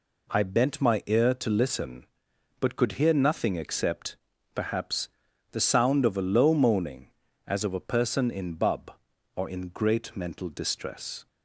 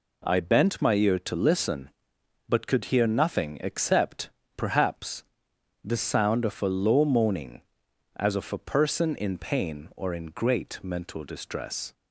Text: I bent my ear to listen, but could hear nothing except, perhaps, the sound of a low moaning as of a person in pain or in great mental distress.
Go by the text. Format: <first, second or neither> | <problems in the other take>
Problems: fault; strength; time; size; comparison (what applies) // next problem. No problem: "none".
second | says "bub" for "pain"; at 8.5 s